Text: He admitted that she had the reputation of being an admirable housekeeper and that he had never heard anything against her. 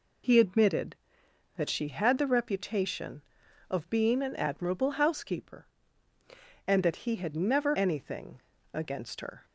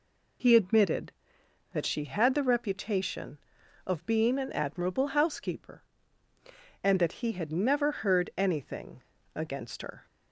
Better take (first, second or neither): second